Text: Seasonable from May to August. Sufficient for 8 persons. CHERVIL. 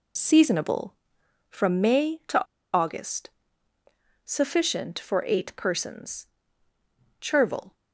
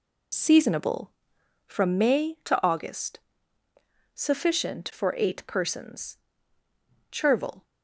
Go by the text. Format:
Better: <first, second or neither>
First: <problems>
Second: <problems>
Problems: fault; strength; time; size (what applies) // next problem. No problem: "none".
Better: second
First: pauses between "to" and "August"; slight; at 2.4 s; 0.31 s long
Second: none